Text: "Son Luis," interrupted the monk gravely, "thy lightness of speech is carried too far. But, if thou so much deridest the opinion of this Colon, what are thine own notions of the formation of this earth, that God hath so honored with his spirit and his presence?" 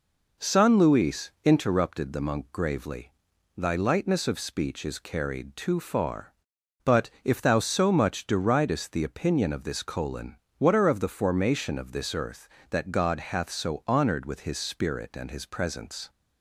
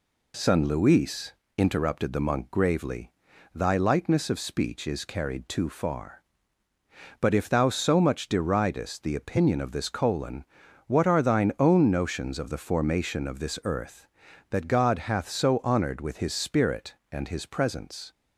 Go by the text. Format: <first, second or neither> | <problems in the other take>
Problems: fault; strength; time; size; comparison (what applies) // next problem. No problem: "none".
second | skips "thine own notions"; at 10.8 s